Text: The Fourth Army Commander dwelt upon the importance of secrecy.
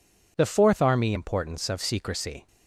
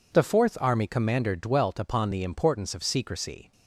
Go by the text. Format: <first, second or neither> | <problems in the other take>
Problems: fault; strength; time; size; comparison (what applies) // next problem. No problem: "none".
second | skips "Commander dwelt upon the"; at 1.1 s